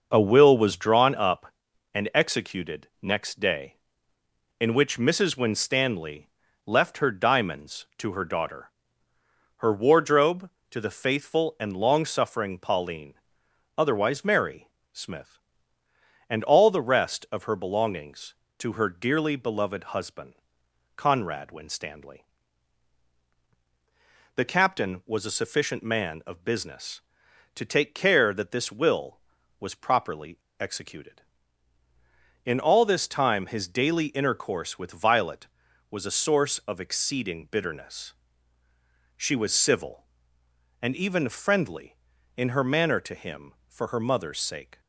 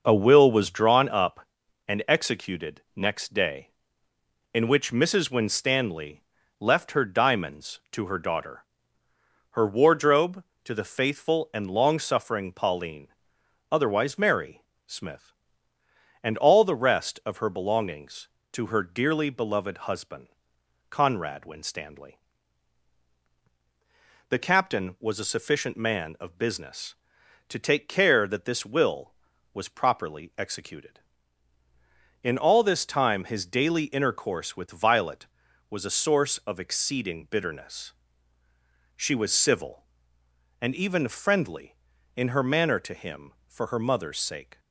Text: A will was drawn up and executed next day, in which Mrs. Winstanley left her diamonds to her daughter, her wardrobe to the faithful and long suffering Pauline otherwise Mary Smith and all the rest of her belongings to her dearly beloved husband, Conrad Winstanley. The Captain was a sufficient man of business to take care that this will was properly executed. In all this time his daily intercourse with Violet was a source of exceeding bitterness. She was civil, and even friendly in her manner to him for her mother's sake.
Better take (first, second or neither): second